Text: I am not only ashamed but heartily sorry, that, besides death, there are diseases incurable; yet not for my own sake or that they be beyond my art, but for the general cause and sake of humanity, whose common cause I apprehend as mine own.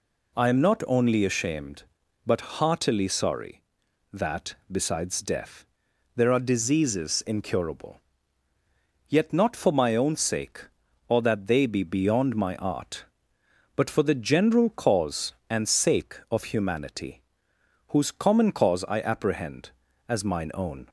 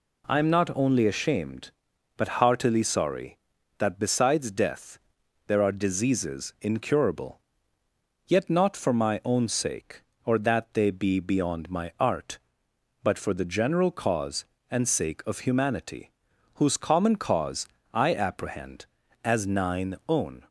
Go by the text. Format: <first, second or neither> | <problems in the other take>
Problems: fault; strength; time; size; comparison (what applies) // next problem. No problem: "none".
first | pauses between "cause" and "I"; slight; at 17.6 s; 0.26 s long // says "nine" for "mine"; at 19.4 s